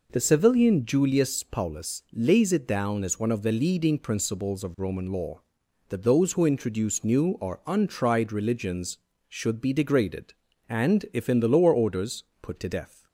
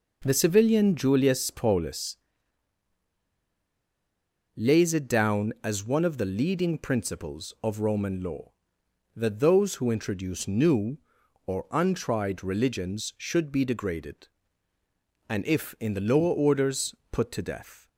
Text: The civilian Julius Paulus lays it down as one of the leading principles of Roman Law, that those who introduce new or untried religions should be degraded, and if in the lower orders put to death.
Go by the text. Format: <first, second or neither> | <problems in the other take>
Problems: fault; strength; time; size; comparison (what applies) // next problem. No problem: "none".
first | pauses between "Paulus" and "lays"; strong; at 2.1 s; 2.4 s long // pauses between "orders" and "put"; slight; at 16.9 s; 0.16 s long; slight in the first